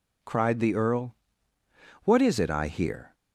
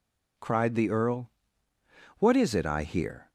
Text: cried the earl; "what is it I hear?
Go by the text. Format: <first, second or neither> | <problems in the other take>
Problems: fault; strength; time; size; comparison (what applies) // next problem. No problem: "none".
neither | none